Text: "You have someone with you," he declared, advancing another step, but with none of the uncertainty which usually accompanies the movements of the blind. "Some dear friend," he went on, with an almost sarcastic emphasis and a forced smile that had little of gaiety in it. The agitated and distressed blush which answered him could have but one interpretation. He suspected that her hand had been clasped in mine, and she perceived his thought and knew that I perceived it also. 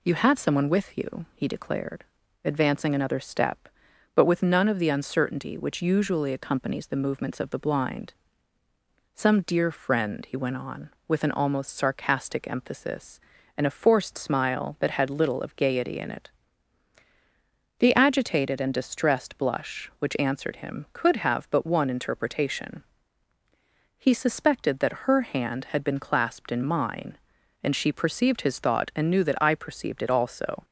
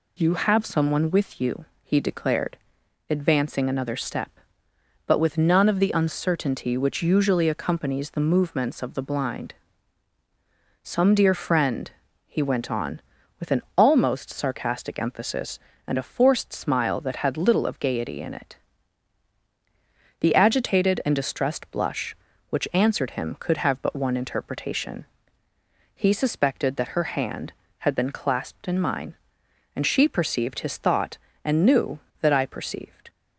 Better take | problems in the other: first | stops before "it also"; at 33.0 s

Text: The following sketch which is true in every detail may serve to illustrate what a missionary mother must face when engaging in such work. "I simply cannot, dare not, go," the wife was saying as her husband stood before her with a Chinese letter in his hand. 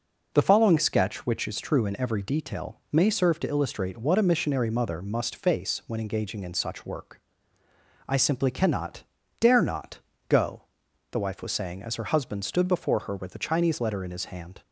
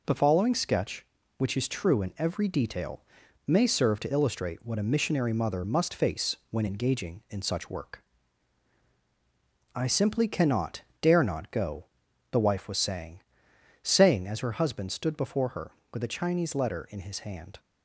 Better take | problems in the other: first | pauses between "detail" and "may"; noticeable; at 3.0 s; 0.46 s long // says "saying" twice; at 13.8 s

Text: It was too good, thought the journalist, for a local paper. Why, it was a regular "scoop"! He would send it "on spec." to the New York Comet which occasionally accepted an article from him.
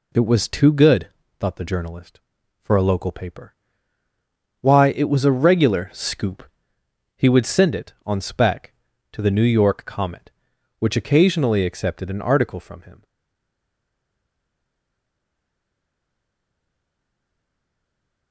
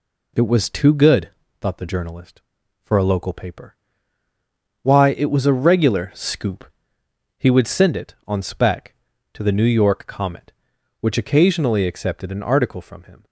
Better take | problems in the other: second | stays silent after the last word; strong; from 13.0 s on; 5.3 s long

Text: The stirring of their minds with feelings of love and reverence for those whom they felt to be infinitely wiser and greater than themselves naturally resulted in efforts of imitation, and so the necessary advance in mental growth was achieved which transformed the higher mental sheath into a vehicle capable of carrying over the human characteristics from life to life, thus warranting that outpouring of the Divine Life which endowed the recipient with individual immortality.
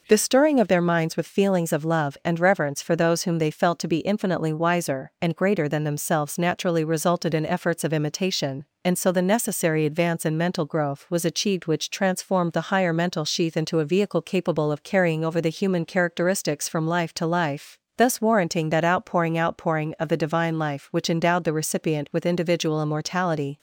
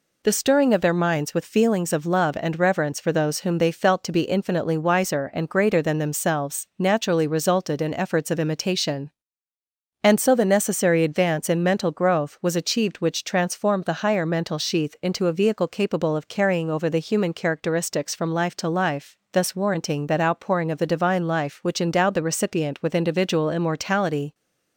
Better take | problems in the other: second | says "outpouring" twice; at 19.3 s

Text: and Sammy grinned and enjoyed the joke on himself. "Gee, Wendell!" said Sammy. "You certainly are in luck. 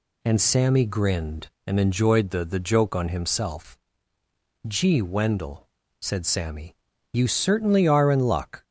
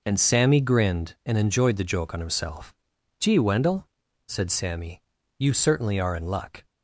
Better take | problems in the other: second | says "the" twice; at 2.4 s

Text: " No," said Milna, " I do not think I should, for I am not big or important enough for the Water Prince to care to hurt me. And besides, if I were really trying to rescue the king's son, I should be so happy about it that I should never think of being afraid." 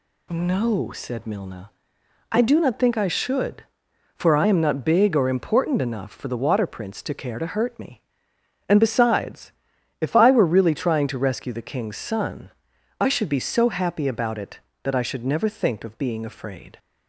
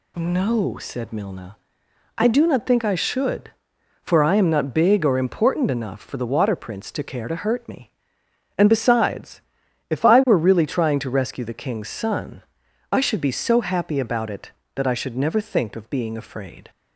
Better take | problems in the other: neither | none

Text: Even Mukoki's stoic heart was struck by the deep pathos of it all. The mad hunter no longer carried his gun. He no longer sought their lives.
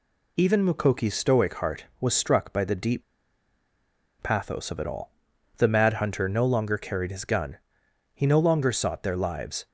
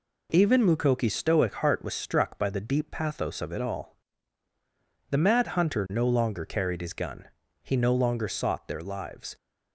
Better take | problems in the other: second | pauses between "deep" and "pathos"; at 3.0 s; 1.1 s long

